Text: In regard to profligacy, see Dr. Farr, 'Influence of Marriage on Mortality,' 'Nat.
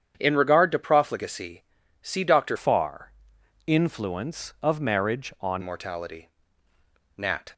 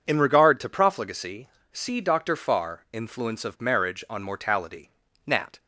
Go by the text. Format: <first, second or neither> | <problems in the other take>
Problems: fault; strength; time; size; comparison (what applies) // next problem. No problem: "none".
second | starts louder than the rest; strong; until 1.1 s; 8.5 dB // changes voice from "Farr" to "on"; from 2.5 to 5.6 s; 3.1 s long